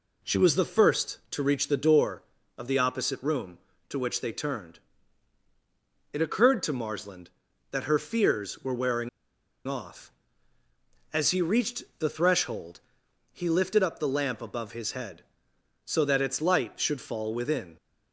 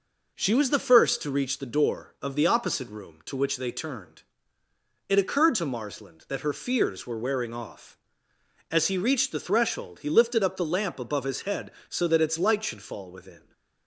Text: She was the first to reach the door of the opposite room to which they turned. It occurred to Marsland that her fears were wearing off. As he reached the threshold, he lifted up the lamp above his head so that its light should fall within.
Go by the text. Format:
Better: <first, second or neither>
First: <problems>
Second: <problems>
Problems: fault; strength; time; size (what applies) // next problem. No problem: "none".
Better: second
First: pauses between "wearing" and "off"; noticeable; at 9.0 s; 0.59 s long // pauses between "reached" and "the"; slight; at 11.8 s; 0.16 s long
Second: none